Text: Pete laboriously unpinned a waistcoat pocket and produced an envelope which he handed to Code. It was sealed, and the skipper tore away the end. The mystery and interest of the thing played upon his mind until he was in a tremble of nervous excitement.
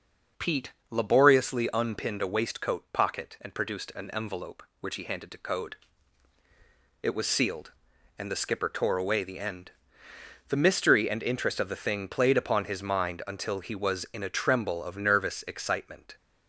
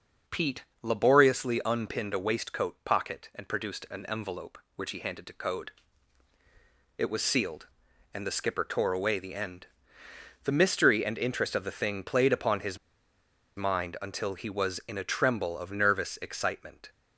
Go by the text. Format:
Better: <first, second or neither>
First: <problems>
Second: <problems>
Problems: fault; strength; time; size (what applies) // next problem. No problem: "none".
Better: first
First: pauses between "Pete" and "laboriously"; slight; at 0.7 s; 0.18 s long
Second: pauses between "Pete" and "laboriously"; slight; at 0.6 s; 0.18 s long // pauses between "his" and "mind"; noticeable; at 12.7 s; 0.80 s long